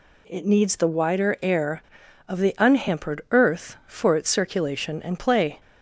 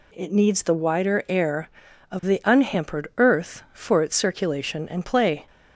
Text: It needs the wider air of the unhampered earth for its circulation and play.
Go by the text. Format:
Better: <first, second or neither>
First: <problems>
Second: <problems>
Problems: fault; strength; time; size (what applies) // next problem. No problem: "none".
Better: neither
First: none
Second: none